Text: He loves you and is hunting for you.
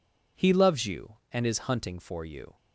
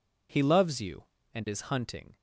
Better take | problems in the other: first | stops before "for you"; at 2.1 s

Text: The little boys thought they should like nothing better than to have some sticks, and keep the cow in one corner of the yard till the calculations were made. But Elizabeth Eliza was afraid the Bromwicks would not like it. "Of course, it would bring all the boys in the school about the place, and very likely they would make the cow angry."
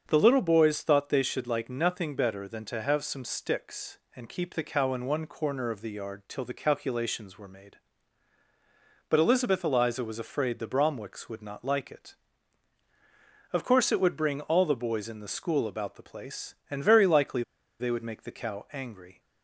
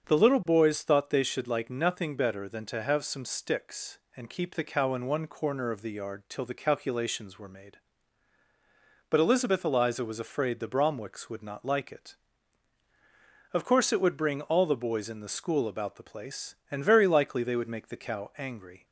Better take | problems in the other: second | starts louder than the rest; until 1.0 s; 7 dB; also in the second // pauses between "likely" and "they"; at 17.4 s; 0.37 s long

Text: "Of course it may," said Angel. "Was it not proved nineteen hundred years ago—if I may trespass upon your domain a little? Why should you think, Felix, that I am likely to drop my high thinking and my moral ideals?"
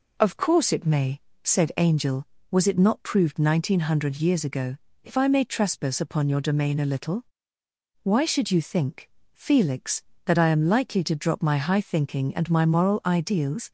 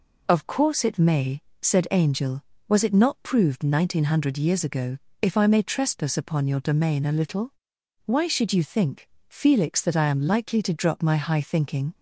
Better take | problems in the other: first | stops before "and my moral ideals"; at 11.9 s

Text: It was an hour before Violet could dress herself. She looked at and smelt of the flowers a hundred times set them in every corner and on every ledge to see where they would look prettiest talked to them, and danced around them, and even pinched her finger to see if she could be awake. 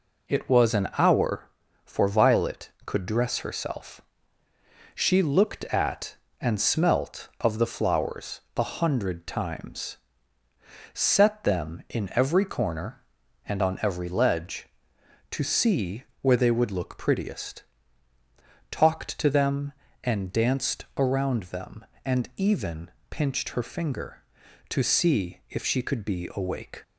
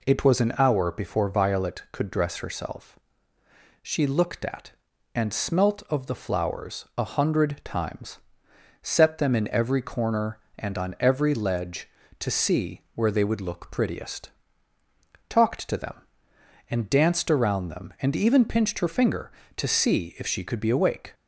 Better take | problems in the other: second | says "for" for "before"; at 1.8 s // pauses between "flowers" and "a"; slight; at 8.4 s; 0.16 s long // pauses between "times" and "set"; noticeable; at 9.9 s; 0.96 s long; noticeable in the second // pauses between "see" and "where"; slight; at 16.0 s; 0.18 s long // pauses between "prettiest" and "talked"; at 17.6 s; 1.0 s long; noticeable in the second // pauses between "even" and "pinched"; slight; at 22.9 s; 0.20 s long

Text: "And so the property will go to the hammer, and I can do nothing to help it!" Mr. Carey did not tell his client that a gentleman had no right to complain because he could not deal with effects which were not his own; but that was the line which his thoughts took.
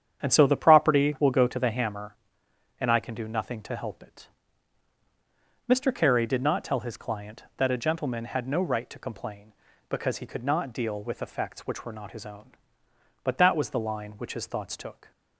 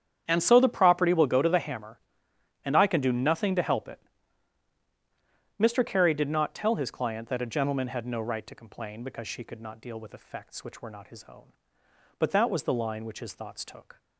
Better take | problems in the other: first | starts louder than the rest; strong; until 1.2 s; 9 dB; strong in the first // says "she" for "he"; at 9.2 s

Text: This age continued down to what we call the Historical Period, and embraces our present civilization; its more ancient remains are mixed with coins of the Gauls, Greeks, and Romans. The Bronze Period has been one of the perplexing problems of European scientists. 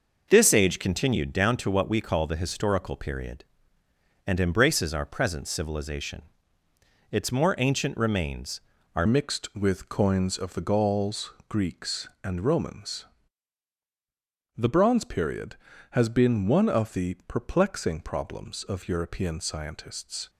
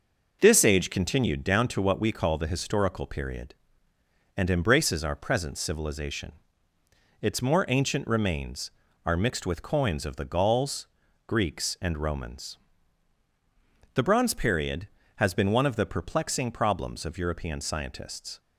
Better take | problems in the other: second | changes voice at "mixed"; from 9.0 s on; 11.2 s long

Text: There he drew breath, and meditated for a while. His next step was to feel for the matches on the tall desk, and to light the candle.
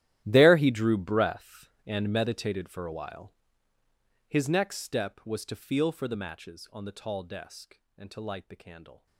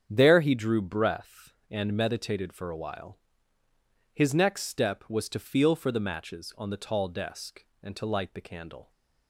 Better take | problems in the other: second | gets quieter; strong; throughout; 19 dB // starts louder than the rest; strong; until 1.2 s; 13 dB; strong in the second

